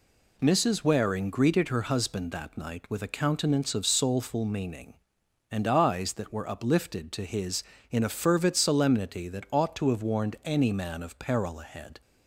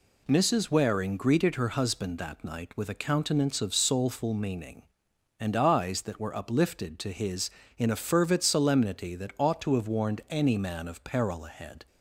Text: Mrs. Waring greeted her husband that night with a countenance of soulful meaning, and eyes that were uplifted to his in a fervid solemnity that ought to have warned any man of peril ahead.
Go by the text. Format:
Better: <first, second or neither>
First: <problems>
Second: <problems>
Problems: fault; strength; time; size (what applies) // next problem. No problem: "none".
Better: neither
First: none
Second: none